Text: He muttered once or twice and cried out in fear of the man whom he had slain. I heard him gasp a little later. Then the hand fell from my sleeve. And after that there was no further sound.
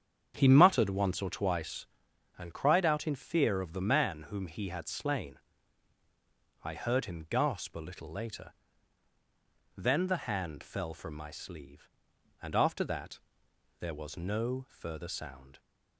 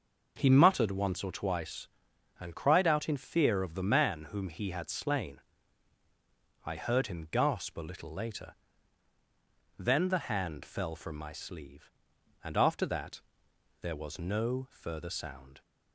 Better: second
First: starts louder than the rest; strong; until 2.0 s; 8 dB // pauses between "that" and "there"; noticeable; at 13.1 s; 0.60 s long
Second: pauses between "that" and "there"; noticeable; at 13.2 s; 0.60 s long

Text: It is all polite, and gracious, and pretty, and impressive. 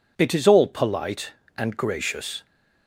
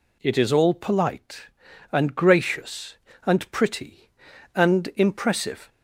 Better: second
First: stops before "and pretty and impressive"; at 2.4 s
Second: none

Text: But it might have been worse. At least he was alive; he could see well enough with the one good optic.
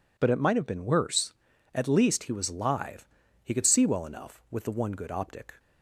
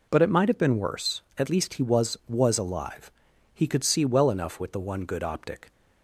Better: first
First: none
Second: says "was" twice; at 2.2 s

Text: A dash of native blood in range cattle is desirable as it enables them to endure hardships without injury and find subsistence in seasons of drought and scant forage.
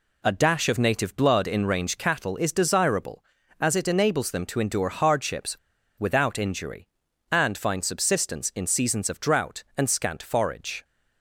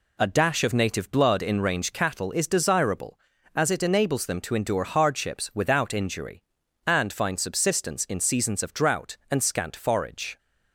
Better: second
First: pauses between "hardships" and "without"; at 5.5 s; 0.40 s long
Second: none

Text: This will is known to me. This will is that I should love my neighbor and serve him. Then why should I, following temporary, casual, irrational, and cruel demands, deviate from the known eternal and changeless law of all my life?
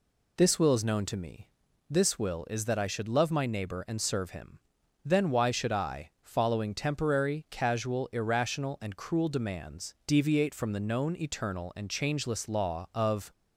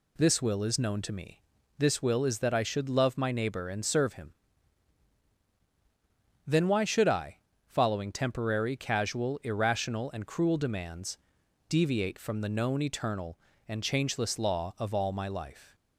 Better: second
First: stops before "all my life"; at 13.3 s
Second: none

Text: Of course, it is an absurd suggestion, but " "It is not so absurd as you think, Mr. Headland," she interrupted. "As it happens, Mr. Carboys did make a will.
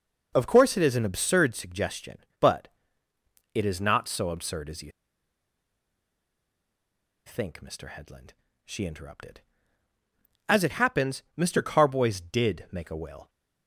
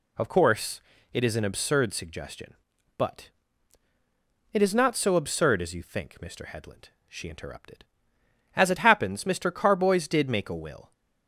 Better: second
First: pauses between "you" and "think"; strong; at 4.9 s; 2.3 s long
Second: none

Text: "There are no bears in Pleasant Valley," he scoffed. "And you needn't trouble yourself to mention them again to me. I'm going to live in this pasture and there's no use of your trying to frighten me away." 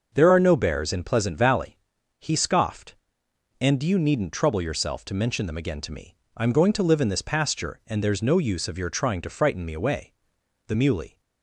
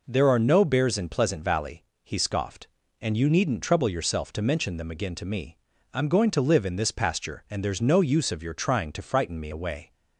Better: second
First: goes on to say "The Muley"; from 10.6 s on; 0.53 s long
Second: none

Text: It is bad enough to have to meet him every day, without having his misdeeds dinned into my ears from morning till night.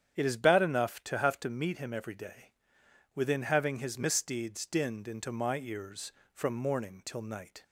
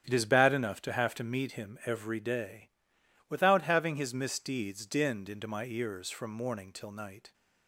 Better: second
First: starts louder than the rest; strong; until 1.2 s; 9 dB // says "within" for "without"; at 3.1 s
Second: starts louder than the rest; strong; until 1.0 s; 9 dB

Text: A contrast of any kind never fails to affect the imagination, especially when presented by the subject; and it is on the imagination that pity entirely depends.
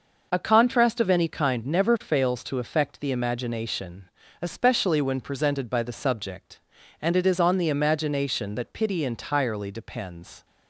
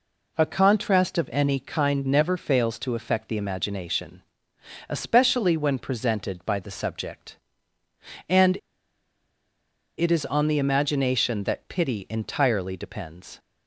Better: first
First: none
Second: pauses between "and" and "it"; strong; at 8.5 s; 1.4 s long

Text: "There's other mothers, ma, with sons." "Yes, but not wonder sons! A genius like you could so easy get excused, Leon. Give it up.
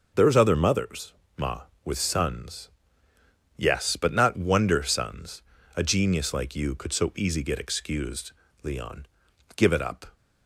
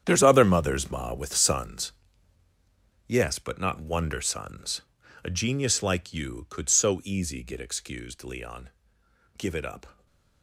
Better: first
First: none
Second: gets quieter; strong; throughout; 15.5 dB // stays silent after the last word; slight; from 9.9 s on; 0.5 s long

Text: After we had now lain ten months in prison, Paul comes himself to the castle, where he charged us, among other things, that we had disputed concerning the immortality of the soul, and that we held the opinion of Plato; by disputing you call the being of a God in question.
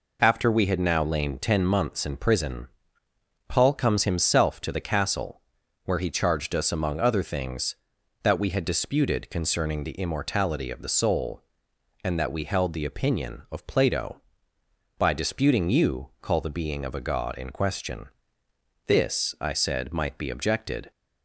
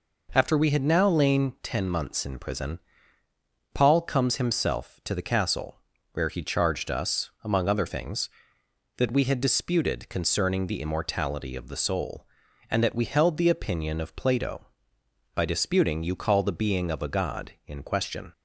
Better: second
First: goes on to say "This I said might be objected"; strong; from 18.8 s on; 2.0 s long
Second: none

